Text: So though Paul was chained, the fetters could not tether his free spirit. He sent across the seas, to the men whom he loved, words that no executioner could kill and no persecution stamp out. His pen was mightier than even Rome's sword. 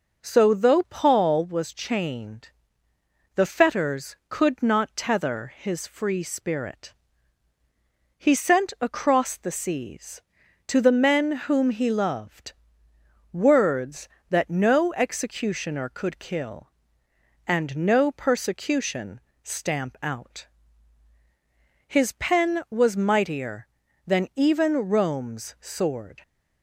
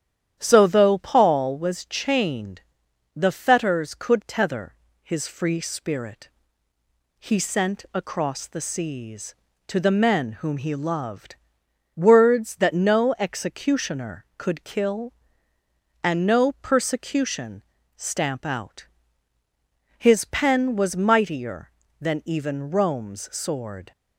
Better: first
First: pauses between "persecution" and "stamp"; slight; at 19.2 s; 0.22 s long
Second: starts louder than the rest; strong; until 1.4 s; 10 dB // skips "not"; at 4.2 s // pauses between "tether" and "his"; slight; at 4.7 s; 0.30 s long // pauses between "persecution" and "stamp"; slight; at 17.6 s; 0.34 s long

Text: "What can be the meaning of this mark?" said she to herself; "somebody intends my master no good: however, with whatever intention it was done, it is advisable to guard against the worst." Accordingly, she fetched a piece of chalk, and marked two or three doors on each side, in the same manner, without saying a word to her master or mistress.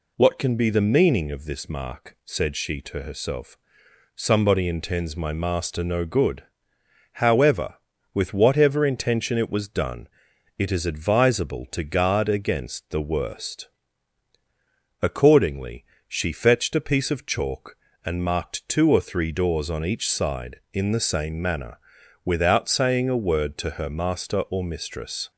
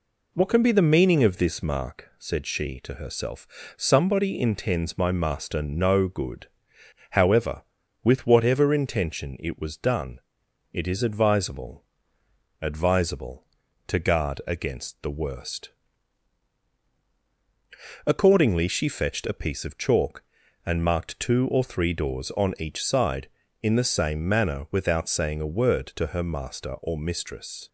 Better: first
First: none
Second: says "advisable" twice; at 12.5 s

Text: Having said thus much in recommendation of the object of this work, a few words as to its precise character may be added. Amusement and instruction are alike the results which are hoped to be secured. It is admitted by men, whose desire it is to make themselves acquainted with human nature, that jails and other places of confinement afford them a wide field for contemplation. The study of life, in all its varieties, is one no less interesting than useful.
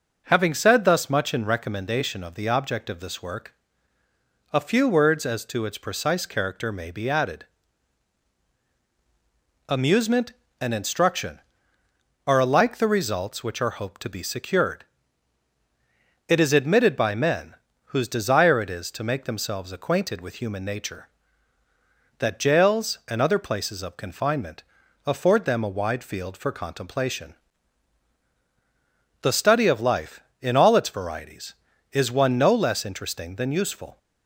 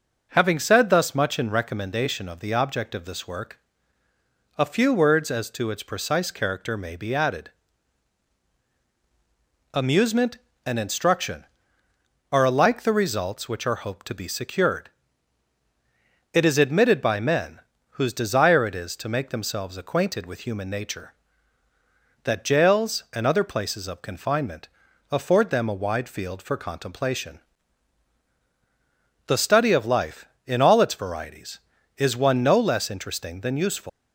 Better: first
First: pauses between "confinement" and "afford"; at 24.6 s; 0.42 s long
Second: pauses between "confinement" and "afford"; at 24.6 s; 0.42 s long // leaves "useful" unfinished; at 33.8 s; 135 ms

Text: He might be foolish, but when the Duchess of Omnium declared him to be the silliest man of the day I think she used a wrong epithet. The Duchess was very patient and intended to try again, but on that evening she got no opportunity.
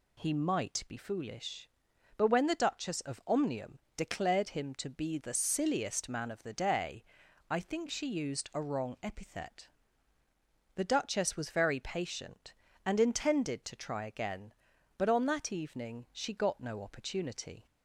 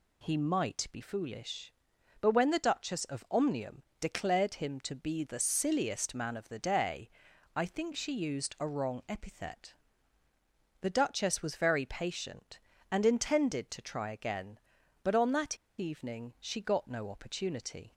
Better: first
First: pauses between "Omnium" and "declared"; slight; at 3.7 s; 0.16 s long // pauses between "day" and "I"; noticeable; at 7.0 s; 0.46 s long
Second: pauses between "Omnium" and "declared"; slight; at 3.8 s; 0.16 s long // pauses between "day" and "I"; noticeable; at 7.0 s; 0.46 s long // pauses between "that" and "evening"; slight; at 15.5 s; 0.22 s long

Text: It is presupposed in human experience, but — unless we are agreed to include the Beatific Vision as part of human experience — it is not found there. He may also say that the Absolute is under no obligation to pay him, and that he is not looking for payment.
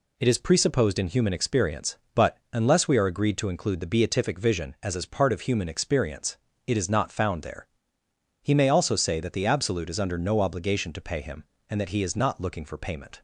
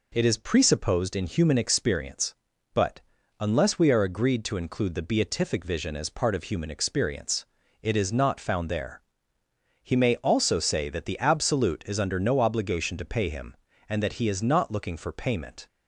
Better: second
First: says "as" twice; at 4.9 s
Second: none

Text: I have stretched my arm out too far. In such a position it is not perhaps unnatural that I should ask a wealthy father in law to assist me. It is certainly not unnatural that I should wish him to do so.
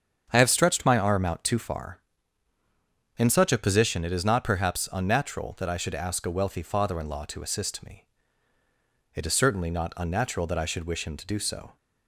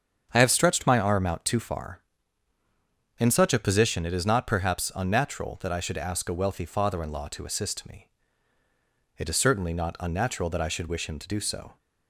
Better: neither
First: starts louder than the rest; strong; until 1.3 s; 7 dB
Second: starts louder than the rest; strong; until 1.3 s; 7 dB

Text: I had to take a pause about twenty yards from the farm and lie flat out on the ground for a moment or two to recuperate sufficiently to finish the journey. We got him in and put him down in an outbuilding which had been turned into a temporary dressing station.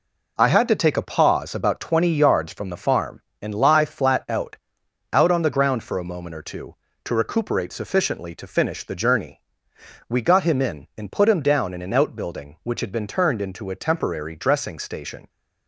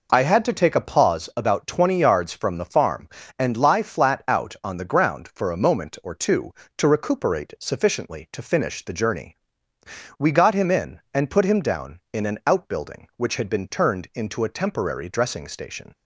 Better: second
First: says "out" twice; at 5.1 s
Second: none

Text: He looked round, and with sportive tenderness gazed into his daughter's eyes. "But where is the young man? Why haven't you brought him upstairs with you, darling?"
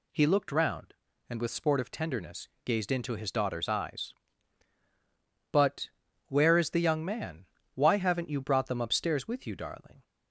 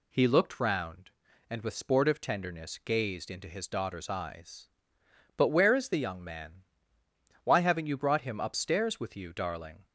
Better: second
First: pauses between "tenderness" and "gazed"; slight; at 2.4 s; 0.16 s long // pauses between "But" and "where"; at 5.8 s; 0.38 s long // says "them" for "him"; at 8.6 s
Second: none

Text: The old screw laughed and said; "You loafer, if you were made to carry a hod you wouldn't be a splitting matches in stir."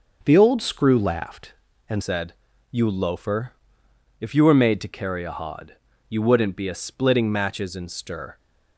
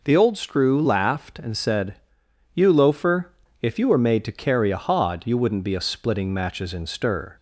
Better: second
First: starts louder than the rest; until 1.2 s; 6 dB // changes voice at "said"; from 2.0 s on; 6.3 s long // pauses between "hod" and "you"; slight; at 5.7 s; 0.34 s long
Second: none

